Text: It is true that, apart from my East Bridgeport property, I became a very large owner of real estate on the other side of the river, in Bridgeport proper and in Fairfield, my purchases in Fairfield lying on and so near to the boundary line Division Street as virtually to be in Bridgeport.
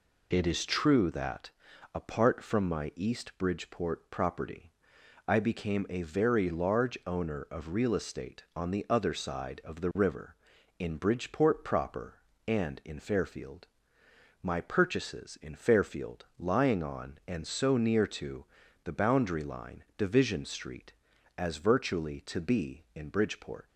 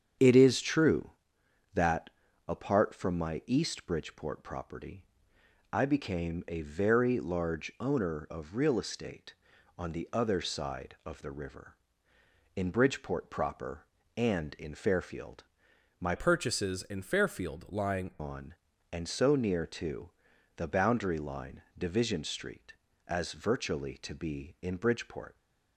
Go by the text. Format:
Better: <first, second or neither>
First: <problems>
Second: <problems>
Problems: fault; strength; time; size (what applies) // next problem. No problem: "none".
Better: first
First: pauses between "to" and "the"; at 18.4 s; 0.40 s long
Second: starts louder than the rest; strong; until 1.8 s; 8 dB // changes voice from "purchases" to "lying"; from 16.1 to 18.1 s; 2.0 s long // pauses between "to" and "the"; noticeable; at 20.0 s; 0.46 s long // pauses between "line" and "Division"; slight; at 21.6 s; 0.16 s long